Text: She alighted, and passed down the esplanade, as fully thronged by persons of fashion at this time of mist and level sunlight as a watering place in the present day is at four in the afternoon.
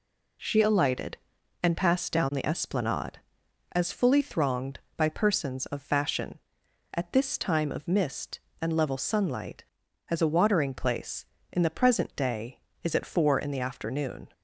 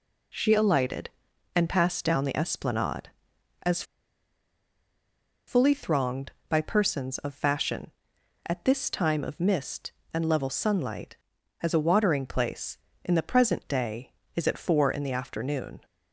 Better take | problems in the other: first | pauses between "as" and "fully"; strong; at 3.8 s; 1.6 s long

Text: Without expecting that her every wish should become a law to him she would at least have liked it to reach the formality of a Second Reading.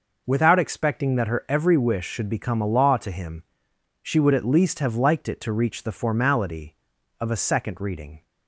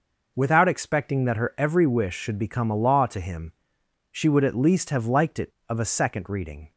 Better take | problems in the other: first | pauses between "him" and "she"; noticeable; at 3.5 s; 0.60 s long; noticeable in the first // skips "to reach the formality"; at 5.5 s

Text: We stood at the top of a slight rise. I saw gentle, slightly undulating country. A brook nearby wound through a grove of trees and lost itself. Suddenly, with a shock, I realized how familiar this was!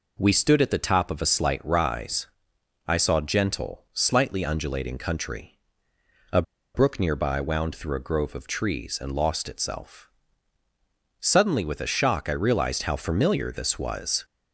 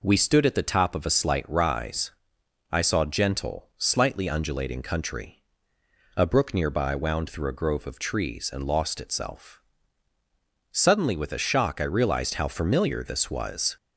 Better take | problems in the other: second | pauses between "A" and "brook"; slight; at 6.4 s; 0.32 s long

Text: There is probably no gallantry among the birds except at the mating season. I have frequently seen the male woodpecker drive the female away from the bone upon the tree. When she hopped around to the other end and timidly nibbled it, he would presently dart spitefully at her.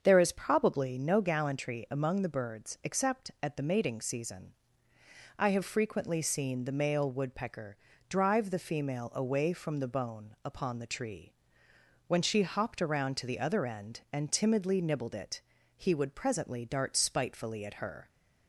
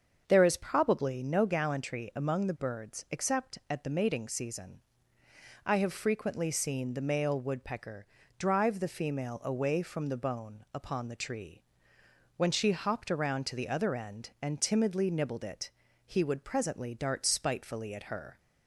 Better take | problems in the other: neither | starts louder than the rest; the same in both // pauses between "woodpecker" and "drive"; slight; the same in both

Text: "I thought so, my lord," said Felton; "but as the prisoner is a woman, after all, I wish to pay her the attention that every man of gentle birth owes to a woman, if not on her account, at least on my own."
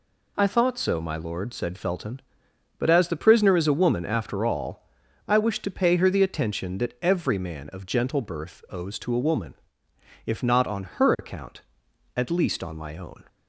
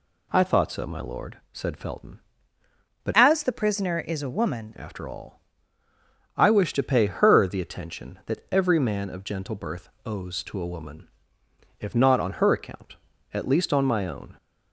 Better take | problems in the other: first | changes voice from "as" to "woman"; from 3.1 to 4.7 s; 1.6 s long // pauses between "birth" and "owes"; slight; at 9.8 s; 0.16 s long

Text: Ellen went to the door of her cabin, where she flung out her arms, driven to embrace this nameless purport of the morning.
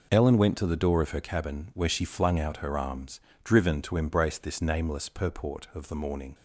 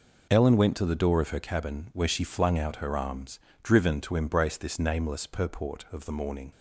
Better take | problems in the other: neither | none

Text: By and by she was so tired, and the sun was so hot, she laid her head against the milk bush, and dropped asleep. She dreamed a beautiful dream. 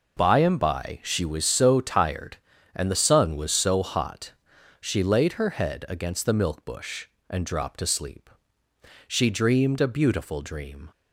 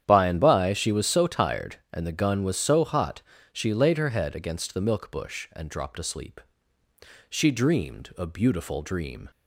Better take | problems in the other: first | starts louder than the rest; strong; until 1.0 s; 9.5 dB // says "gun" for "sun"; at 2.1 s

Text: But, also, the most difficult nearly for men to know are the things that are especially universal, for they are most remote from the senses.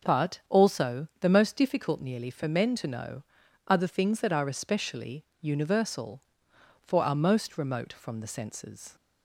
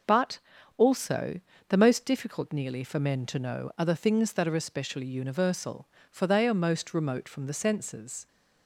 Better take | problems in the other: second | starts louder than the rest; noticeable; until 1.2 s; 6 dB // pauses between "especially" and "universal"; slight; at 5.2 s; 0.16 s long // skips "they"; at 7.0 s

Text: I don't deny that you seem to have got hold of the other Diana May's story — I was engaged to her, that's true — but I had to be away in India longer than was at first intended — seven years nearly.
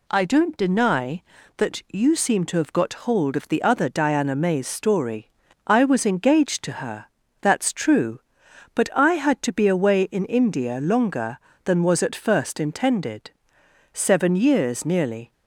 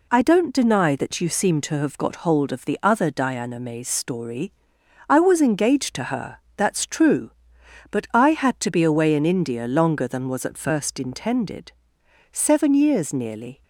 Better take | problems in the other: neither | none

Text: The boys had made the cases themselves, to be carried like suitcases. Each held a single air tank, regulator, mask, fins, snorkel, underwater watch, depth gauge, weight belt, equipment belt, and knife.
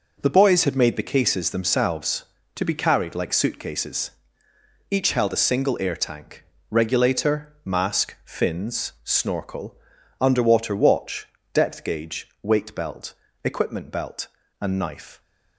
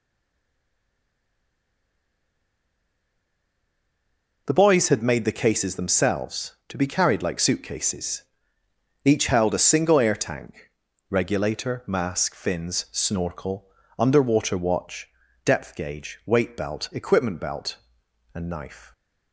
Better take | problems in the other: first | stays silent before the first word; strong; until 4.4 s; 4.4 s long

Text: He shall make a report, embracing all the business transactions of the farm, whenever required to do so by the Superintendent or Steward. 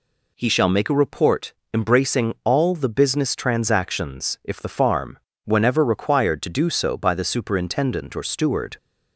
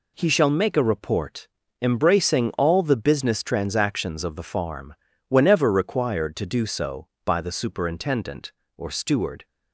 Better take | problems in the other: second | says "if" for "of"; at 4.4 s

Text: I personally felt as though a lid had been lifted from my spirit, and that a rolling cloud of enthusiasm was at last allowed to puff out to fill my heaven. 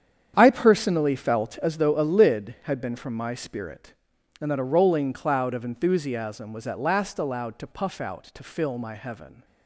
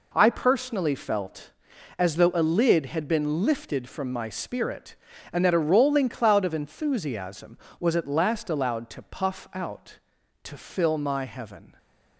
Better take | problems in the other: second | starts louder than the rest; strong; until 1.3 s; 8.5 dB // skips "lifted"; at 2.9 s

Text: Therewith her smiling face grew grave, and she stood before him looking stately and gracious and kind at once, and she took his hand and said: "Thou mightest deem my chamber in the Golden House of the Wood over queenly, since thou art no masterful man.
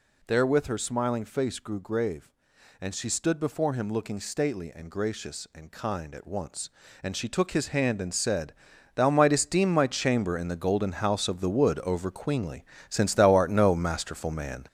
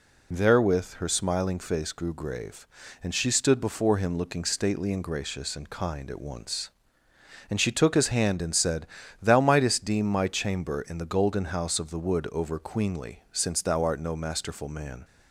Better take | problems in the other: second | gets louder; noticeable; throughout; 6 dB

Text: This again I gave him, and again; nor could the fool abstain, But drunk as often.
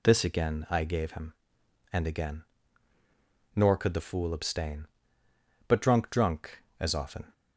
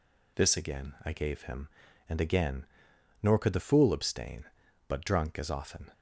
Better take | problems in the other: second | says "drunk" twice; at 6.0 s

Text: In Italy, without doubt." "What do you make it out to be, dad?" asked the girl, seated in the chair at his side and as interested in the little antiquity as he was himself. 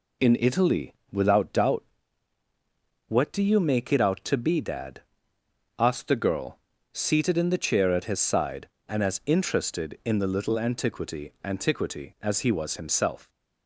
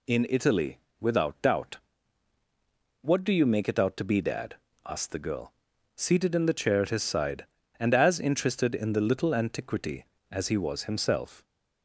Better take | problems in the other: second | says "antiquity" twice; at 11.4 s

